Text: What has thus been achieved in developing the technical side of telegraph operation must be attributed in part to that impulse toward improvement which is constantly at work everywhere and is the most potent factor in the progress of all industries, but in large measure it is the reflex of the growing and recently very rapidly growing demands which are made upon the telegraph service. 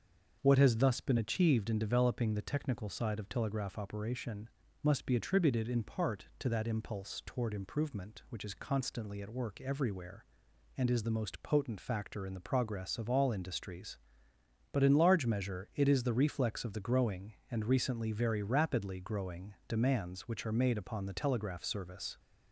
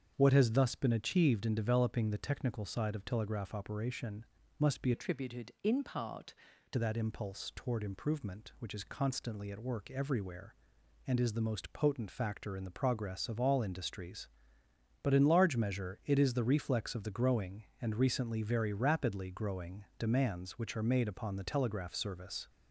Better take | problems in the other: first | starts louder than the rest; strong; until 1.1 s; 7 dB; also in the first // pauses between "operation" and "must"; slight; at 4.2 s; 0.36 s long; slight in the first // changes voice from "attributed" to "to"; from 4.9 to 6.7 s; 1.8 s long

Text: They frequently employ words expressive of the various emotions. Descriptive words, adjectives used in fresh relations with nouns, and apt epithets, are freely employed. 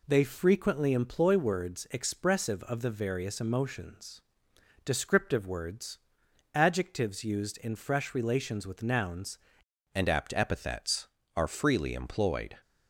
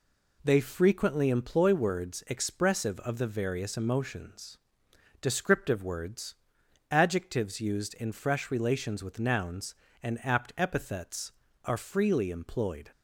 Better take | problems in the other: second | changes voice at "and"; from 9.9 s on; 2.6 s long

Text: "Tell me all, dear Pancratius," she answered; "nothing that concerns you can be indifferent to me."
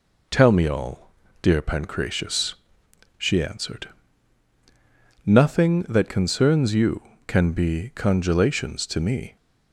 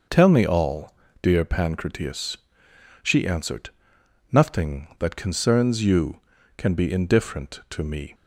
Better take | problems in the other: second | says "congelations" for "indifferent"; at 7.9 s

